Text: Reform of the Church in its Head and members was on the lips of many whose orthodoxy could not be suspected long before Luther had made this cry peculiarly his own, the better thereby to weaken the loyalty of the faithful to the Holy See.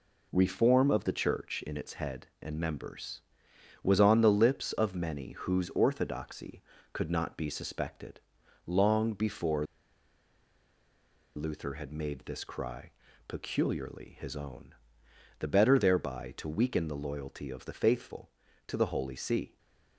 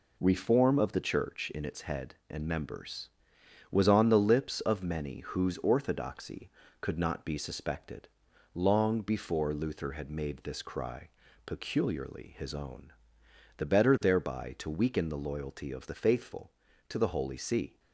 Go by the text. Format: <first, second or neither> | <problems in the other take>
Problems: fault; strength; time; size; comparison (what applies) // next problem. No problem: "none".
second | pauses between "suspected" and "long"; noticeable; at 8.1 s; 0.46 s long; noticeable in the second // pauses between "before" and "Luther"; strong; at 9.6 s; 1.7 s long // pauses between "cry" and "peculiarly"; slight; at 12.9 s; 0.34 s long; slight in the second // stays silent after the last word; slight; from 19.4 s on; 0.5 s long